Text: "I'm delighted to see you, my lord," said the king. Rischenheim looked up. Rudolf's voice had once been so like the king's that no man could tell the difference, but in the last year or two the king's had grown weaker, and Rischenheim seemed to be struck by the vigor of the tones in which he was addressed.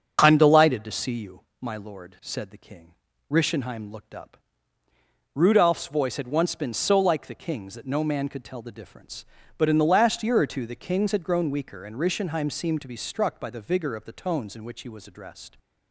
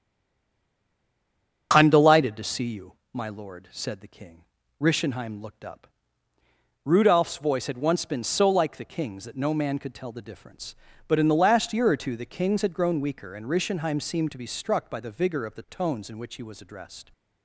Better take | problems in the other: first | stays silent before the first word; noticeable; until 1.7 s; 1.7 s long // starts louder than the rest; until 2.7 s; 6.5 dB; also in the first

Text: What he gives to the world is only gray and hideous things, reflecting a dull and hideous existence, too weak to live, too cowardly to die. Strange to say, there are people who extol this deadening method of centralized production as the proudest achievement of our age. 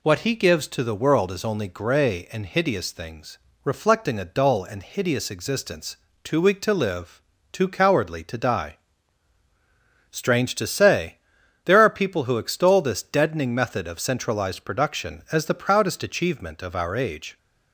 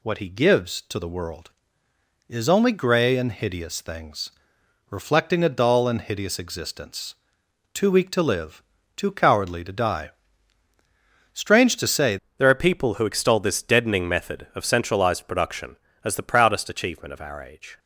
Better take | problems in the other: first | changes voice at "there"; from 12.3 s on; 5.4 s long

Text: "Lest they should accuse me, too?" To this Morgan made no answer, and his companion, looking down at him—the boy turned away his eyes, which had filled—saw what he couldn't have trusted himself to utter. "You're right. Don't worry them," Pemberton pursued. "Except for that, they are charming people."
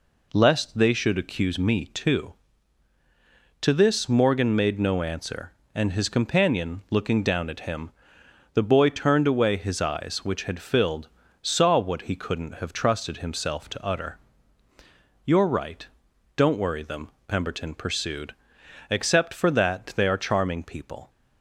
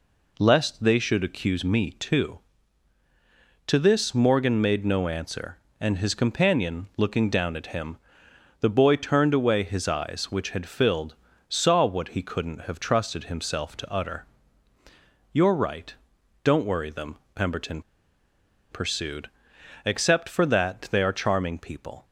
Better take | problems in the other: first | pauses between "Pemberton" and "pursued"; noticeable; at 17.8 s; 0.90 s long

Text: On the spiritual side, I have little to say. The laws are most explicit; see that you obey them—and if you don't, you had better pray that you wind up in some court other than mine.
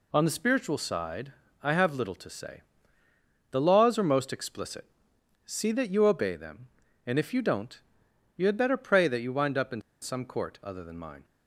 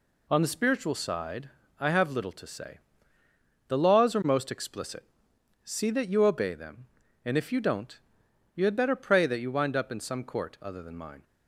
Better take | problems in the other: second | pauses between "in" and "some"; slight; at 9.8 s; 0.21 s long

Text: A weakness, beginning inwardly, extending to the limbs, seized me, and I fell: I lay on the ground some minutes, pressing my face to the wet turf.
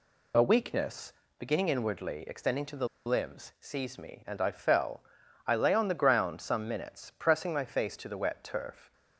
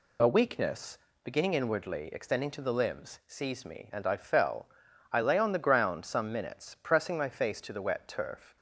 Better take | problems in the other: second | pauses between "the" and "limbs"; slight; at 2.8 s; 0.18 s long

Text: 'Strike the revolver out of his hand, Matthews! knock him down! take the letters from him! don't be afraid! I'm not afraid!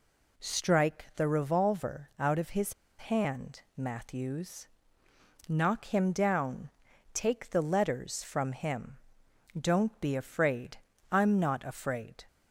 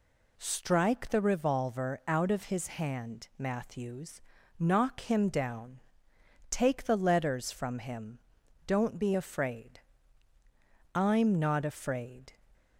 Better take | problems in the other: second | pauses between "his" and "hand"; slight; at 2.7 s; 0.25 s long

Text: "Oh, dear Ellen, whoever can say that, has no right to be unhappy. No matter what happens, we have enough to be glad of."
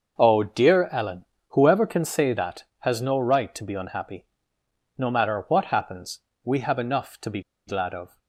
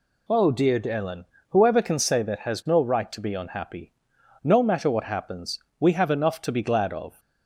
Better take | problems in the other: second | starts louder than the rest; noticeable; until 1.2 s; 6 dB // pauses between "be" and "glad"; slight; at 7.3 s; 0.27 s long

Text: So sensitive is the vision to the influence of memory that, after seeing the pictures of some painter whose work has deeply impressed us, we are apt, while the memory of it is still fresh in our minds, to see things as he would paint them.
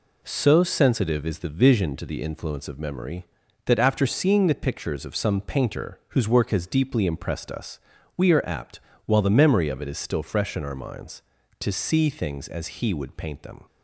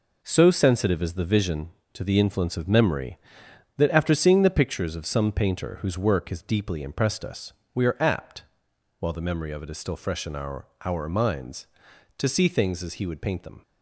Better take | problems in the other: first | says "our" twice; at 10.8 s

